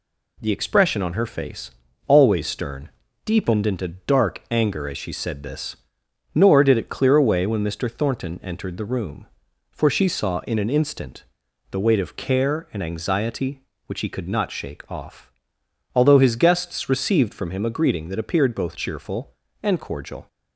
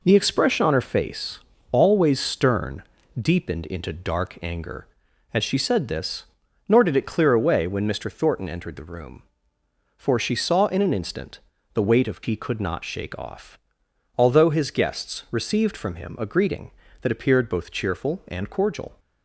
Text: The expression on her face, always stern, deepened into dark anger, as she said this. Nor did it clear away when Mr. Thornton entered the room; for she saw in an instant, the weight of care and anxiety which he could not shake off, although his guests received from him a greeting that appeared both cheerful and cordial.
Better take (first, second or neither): first